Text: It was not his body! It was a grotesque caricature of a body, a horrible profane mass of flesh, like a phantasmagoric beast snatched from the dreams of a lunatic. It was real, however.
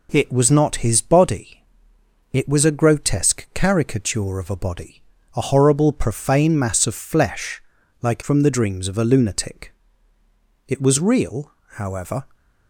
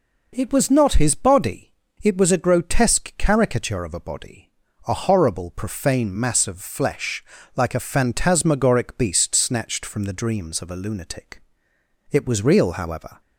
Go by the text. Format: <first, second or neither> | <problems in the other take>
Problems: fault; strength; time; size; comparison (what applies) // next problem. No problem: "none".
second | skips "a phantasmagoric beast snatched"; at 8.2 s